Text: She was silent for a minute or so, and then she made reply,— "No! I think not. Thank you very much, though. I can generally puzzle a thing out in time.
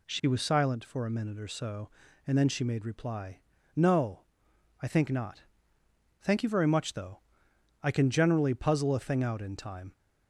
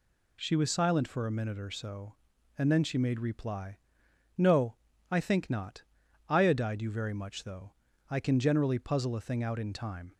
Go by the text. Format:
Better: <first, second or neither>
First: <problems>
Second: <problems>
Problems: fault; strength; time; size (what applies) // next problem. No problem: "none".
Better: first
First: none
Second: says "Iodide" for "Thank"; at 6.2 s